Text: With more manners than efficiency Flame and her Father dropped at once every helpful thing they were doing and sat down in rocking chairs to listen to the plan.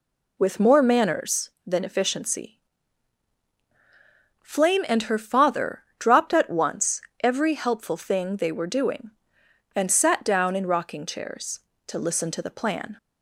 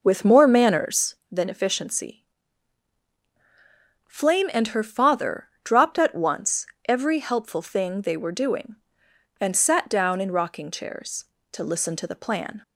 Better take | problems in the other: first | starts louder than the rest; noticeable; until 1.3 s; 5 dB // pauses between "efficiency" and "Flame"; strong; at 2.2 s; 1.8 s long; strong in the first // pauses between "Father" and "dropped"; slight; at 5.4 s; 0.16 s long; slight in the first // pauses between "once" and "every"; slight; at 6.6 s; 0.22 s long; slight in the first

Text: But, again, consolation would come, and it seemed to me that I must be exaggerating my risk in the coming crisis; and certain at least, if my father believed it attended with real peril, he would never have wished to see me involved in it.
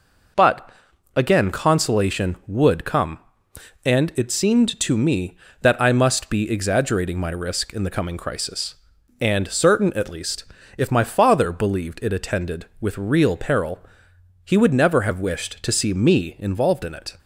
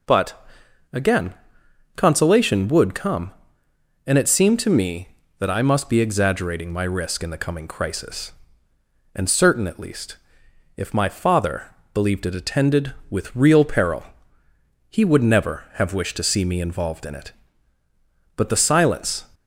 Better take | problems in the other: first | pauses between "father" and "believed"; slight; at 11.6 s; 0.28 s long // goes on to say "But the silence"; noticeable; from 18.3 s on; 0.88 s long

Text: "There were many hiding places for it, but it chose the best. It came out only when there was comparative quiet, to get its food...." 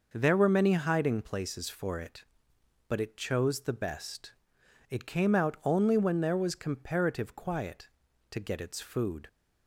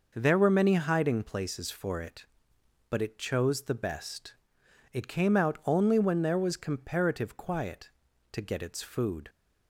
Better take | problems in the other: neither | none

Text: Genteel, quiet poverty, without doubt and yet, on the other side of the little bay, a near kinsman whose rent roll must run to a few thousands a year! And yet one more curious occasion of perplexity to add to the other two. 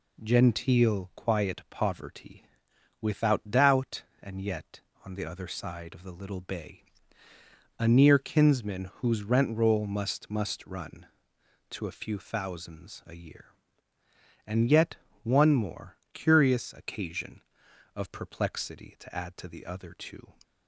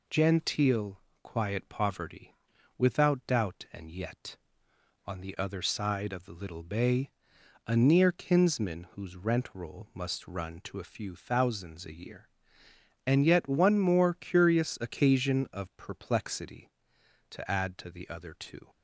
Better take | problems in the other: second | says "must" twice; at 10.3 s // pauses between "yet" and "one"; slight; at 14.9 s; 0.26 s long // pauses between "more" and "curious"; slight; at 15.9 s; 0.18 s long

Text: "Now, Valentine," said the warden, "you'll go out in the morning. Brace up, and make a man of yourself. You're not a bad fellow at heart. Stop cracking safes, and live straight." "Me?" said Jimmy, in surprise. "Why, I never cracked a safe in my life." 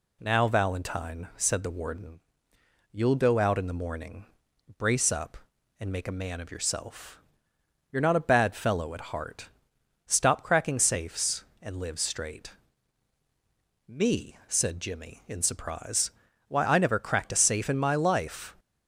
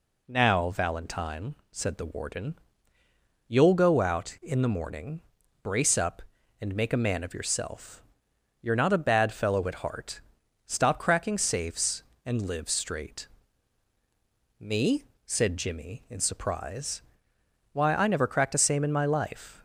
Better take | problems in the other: first | says "same" for "safe"; at 18.5 s

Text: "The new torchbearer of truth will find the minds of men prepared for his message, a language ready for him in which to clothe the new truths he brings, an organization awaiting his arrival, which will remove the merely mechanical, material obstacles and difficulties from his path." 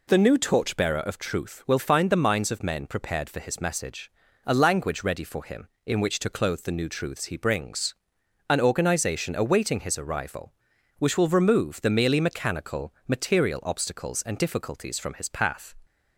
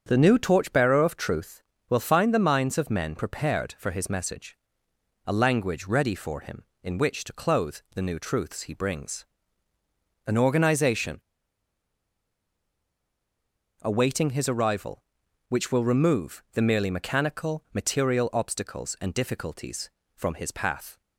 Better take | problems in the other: first | starts louder than the rest; strong; until 1.0 s; 7.5 dB // pauses between "organization" and "awaiting"; strong; at 11.1 s; 2.6 s long

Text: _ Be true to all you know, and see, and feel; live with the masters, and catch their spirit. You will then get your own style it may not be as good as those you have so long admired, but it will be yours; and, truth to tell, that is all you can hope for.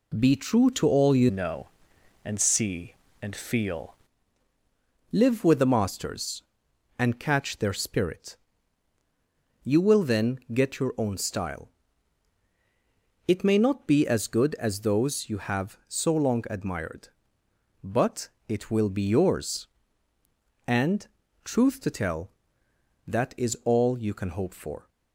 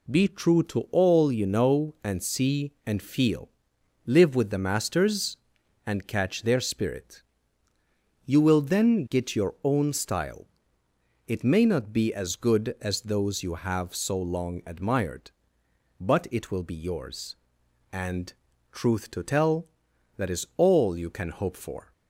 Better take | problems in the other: second | changes voice from "know" to "feel"; from 1.2 to 3.9 s; 2.7 s long // pauses between "style" and "it"; strong; at 11.6 s; 1.6 s long; noticeable in the second // pauses between "but" and "it"; slight; at 18.2 s; 0.22 s long

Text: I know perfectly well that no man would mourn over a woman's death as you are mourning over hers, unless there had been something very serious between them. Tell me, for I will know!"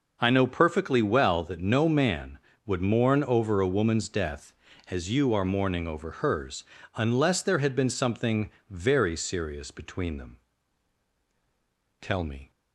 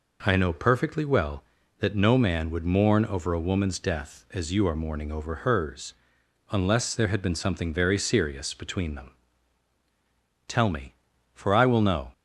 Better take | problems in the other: second | pauses between "something" and "very"; slight; at 8.5 s; 0.20 s long // stops before "for I will know"; at 12.5 s

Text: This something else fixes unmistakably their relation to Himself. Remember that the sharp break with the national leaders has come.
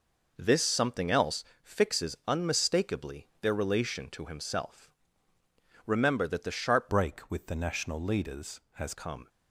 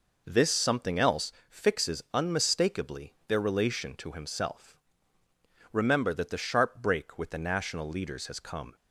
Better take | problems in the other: second | pauses between "else" and "fixes"; slight; at 1.4 s; 0.20 s long; slight in the second // changes voice from "break" to "has"; from 6.8 to 8.9 s; 2.1 s long

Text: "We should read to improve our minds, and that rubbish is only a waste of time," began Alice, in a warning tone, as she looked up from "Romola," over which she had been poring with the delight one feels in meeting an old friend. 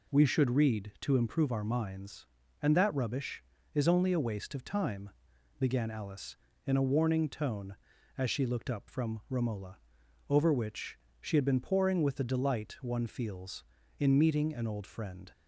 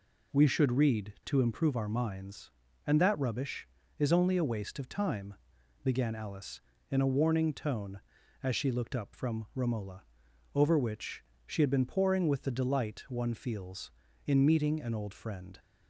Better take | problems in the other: neither | pauses between "which" and "she"; slight; the same in both

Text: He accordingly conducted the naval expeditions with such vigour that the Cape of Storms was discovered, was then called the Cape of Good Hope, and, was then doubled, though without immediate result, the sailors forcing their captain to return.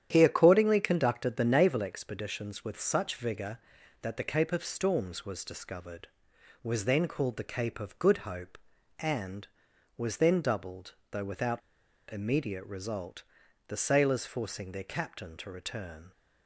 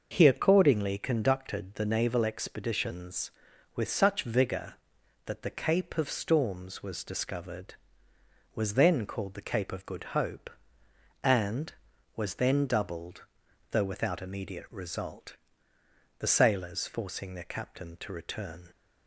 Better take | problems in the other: second | starts louder than the rest; strong; until 1.1 s; 10 dB // pauses between "without" and "immediate"; noticeable; at 11.6 s; 0.50 s long

